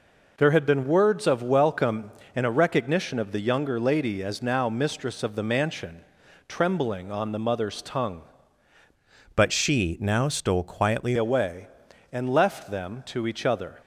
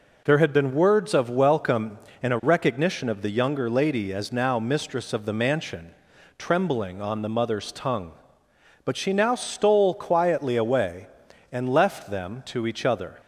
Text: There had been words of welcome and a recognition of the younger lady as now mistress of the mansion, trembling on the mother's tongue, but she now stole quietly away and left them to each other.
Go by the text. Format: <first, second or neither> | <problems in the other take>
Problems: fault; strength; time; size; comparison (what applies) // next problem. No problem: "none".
second | changes voice from "but" to "quietly"; from 9.3 to 11.1 s; 1.8 s long